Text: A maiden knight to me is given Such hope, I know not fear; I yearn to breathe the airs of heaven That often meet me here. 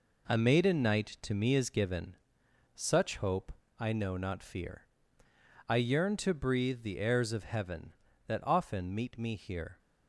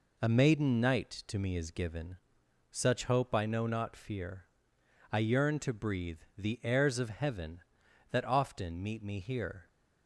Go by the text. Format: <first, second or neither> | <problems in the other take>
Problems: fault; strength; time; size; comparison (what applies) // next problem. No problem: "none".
second | gets quieter; strong; throughout; 7.5 dB // pauses between "given" and "Such"; noticeable; at 2.1 s; 0.58 s long; noticeable in the second